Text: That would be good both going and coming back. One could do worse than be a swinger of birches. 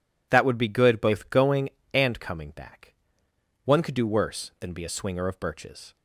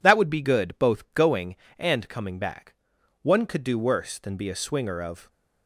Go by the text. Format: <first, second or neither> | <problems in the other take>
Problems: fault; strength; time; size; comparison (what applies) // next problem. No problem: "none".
first | stops before "birches"; at 5.2 s